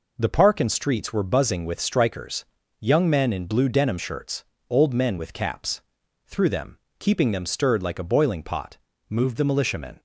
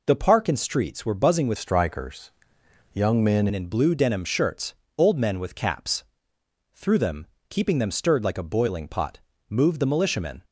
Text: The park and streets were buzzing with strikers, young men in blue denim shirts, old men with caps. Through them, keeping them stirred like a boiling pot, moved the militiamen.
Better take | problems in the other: first | changes voice from "strikers" to "men"; from 1.5 to 3.4 s; 1.9 s long

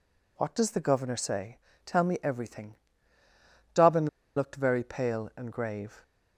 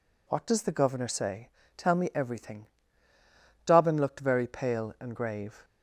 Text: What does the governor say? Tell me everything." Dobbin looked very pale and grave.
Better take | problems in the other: second | pauses between "Dobbin" and "looked"; slight; at 4.0 s; 0.29 s long

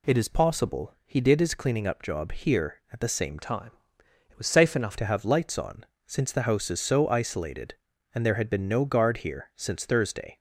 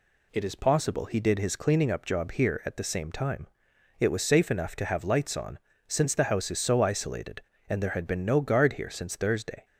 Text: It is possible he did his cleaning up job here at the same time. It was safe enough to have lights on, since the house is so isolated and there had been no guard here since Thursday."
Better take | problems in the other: second | changes voice from "time" to "enough"; from 3.3 to 4.9 s; 1.6 s long

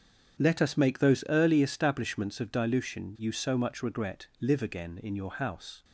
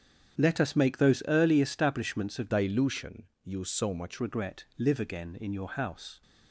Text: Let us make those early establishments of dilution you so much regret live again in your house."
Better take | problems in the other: first | starts louder than the rest; strong; until 1.4 s; 8.5 dB; strong in the first // changes voice from "dilution" to "much"; from 2.5 to 4.1 s; 1.6 s long // pauses between "dilution" and "you"; slight; at 3.2 s; 0.18 s long // pauses between "regret" and "live"; slight; at 4.6 s; 0.16 s long; slight in the first

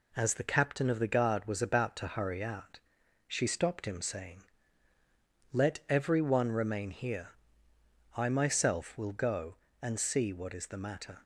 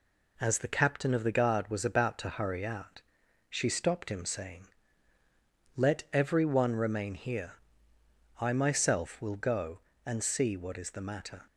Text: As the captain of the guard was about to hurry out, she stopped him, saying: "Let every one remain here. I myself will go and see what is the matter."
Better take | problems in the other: neither | none

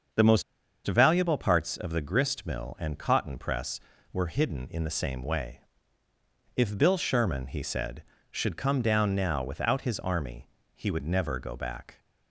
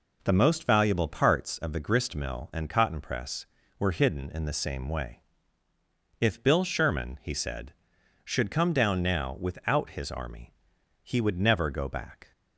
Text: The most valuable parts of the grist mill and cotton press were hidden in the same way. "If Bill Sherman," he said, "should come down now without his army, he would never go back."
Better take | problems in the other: second | starts louder than the rest; until 1.5 s; 7 dB // pauses between "most" and "valuable"; at 0.4 s; 0.44 s long

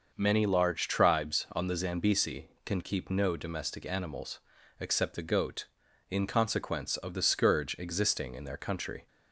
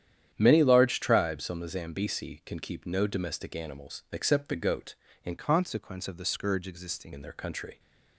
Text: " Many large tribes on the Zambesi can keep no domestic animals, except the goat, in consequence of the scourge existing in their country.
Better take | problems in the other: first | starts louder than the rest; strong; until 1.3 s; 10 dB; noticeable in the first // changes voice from "consequence" to "existing"; from 5.3 to 7.1 s; 1.8 s long

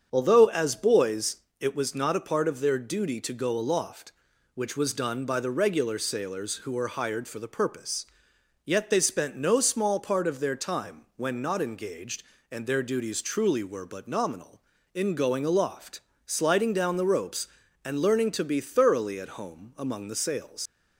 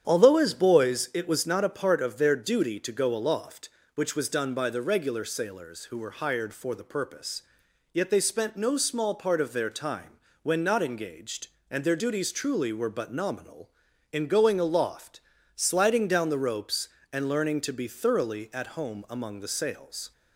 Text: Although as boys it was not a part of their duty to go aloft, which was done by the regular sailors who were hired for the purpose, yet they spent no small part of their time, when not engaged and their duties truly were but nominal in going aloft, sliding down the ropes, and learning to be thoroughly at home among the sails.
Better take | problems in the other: second | starts louder than the rest; strong; until 1.1 s; 7.5 dB; strong in the second // pauses between "boys" and "it"; slight; at 1.3 s; 0.22 s long // leaves "sails" unfinished; at 20.6 s; 100 ms

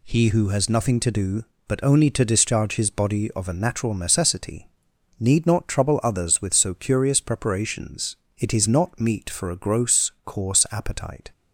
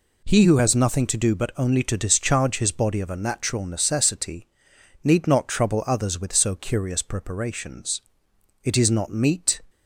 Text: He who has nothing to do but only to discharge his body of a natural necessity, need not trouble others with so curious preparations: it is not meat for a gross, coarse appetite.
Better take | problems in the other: first | stops before "for a gross coarse appetite"; at 9.6 s

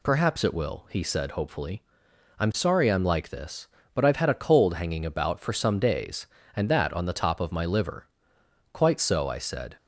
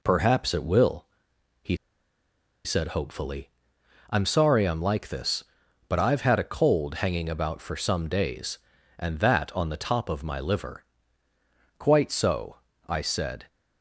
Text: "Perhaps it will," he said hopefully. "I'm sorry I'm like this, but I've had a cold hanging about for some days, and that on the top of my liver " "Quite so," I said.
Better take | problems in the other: first | pauses between "he" and "said"; noticeable; at 1.7 s; 0.89 s long

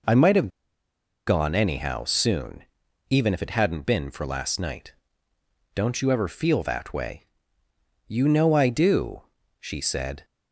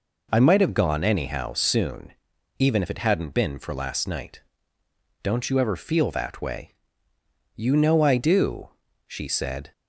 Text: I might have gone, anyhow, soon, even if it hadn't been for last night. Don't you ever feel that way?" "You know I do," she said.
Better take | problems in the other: second | pauses between "have" and "gone"; noticeable; at 0.5 s; 0.76 s long

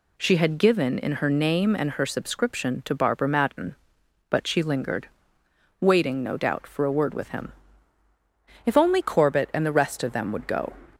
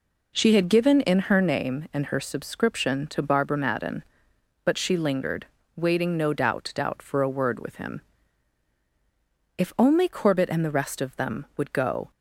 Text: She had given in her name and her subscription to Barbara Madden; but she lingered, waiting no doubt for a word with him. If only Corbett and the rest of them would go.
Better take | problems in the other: first | says "doubt" twice; at 6.7 s

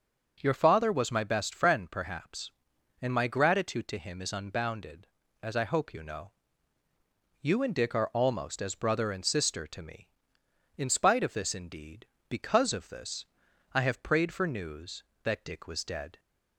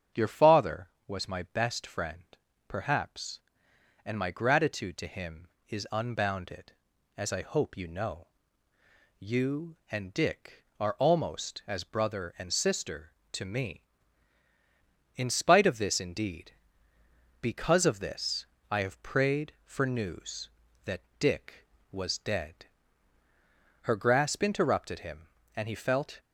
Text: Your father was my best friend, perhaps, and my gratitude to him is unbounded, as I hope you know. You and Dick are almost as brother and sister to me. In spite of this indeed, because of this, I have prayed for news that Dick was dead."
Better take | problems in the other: first | starts louder than the rest; strong; until 1.3 s; 8 dB // pauses between "that" and "Dick"; slight; at 21.0 s; 0.18 s long // goes on to say "Her grasp interrupted him and he felt"; strong; from 23.8 s on; 2.3 s long

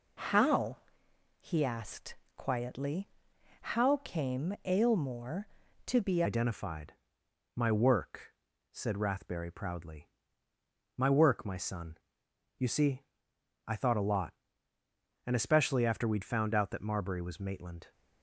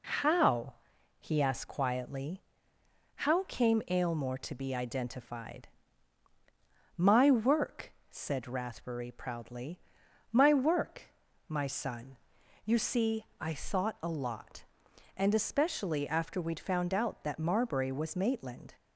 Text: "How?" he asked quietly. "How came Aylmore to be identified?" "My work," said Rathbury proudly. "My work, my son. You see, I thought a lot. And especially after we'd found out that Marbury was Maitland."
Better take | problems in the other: second | pauses between "asked" and "quietly"; slight; at 2.1 s; 0.18 s long // changes voice at "identified"; from 6.2 s on; 11.7 s long

